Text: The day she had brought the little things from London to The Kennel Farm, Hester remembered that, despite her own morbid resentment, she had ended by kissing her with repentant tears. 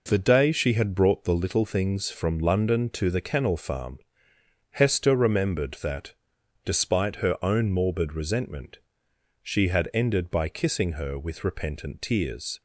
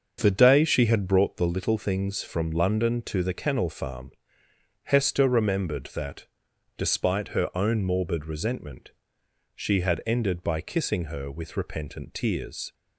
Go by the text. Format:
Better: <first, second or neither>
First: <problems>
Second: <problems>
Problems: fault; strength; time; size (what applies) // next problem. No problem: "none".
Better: first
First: none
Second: starts louder than the rest; until 1.2 s; 6.5 dB